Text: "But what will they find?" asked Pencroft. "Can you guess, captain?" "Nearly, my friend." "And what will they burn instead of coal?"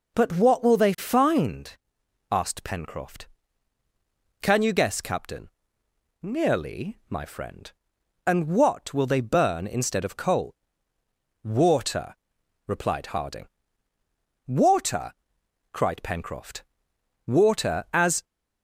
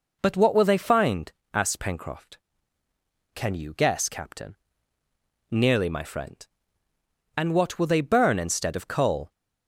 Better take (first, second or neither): second